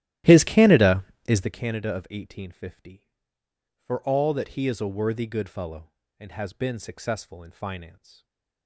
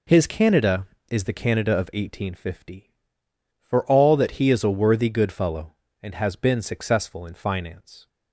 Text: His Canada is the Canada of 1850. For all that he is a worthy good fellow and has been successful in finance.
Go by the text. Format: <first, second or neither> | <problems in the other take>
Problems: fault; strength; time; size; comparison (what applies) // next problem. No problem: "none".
second | starts louder than the rest; strong; until 1.6 s; 12.5 dB // stays silent after the last word; slight; from 7.9 s on; 0.7 s long